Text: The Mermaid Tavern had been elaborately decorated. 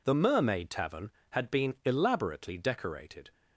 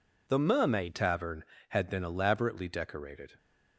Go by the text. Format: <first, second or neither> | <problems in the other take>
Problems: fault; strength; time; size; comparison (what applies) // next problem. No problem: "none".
first | changes voice at "Tavern"; from 0.9 s on; 2.4 s long